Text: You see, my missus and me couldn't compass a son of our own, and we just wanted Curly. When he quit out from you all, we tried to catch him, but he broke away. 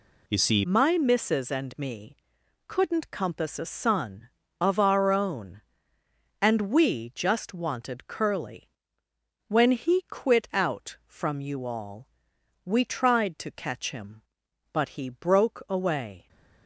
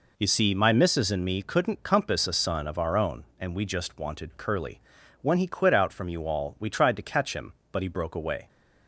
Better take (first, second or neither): second